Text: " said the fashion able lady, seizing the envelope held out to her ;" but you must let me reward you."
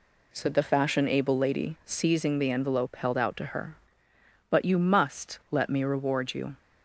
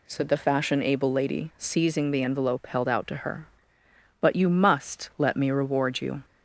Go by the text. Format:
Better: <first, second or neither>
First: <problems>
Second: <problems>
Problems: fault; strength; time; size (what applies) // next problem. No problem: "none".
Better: second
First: gets quieter; strong; throughout; 7.5 dB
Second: none